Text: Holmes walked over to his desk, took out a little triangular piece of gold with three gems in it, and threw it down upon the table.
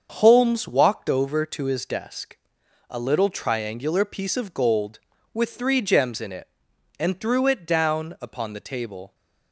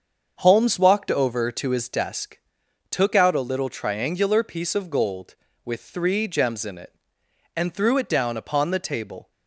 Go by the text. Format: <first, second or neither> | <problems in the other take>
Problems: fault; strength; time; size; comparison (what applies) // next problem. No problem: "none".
second | starts louder than the rest; until 1.1 s; 7 dB; also in the second // skips "took out"; at 2.6 s